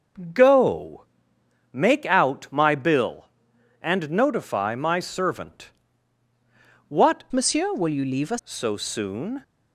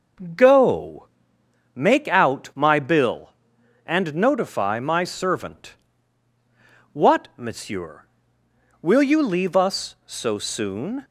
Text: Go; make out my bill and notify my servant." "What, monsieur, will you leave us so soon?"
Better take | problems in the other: second | starts louder than the rest; until 1.9 s; 6 dB // changes voice from "monsieur" to "us"; from 7.3 to 8.3 s; 1.0 s long

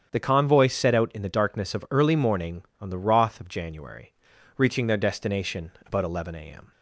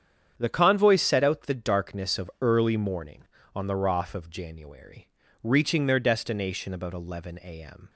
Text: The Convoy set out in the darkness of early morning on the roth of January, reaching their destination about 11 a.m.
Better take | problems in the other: first | starts louder than the rest; strong; until 1.3 s; 8.5 dB; strong in the first // skips "in"; at 1.4 s

